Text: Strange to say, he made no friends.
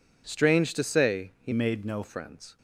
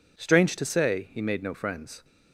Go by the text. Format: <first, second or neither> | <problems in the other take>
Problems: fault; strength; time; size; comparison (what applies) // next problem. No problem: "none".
second | changes voice from "made" to "no"; from 1.5 to 2.0 s; 0.5 s long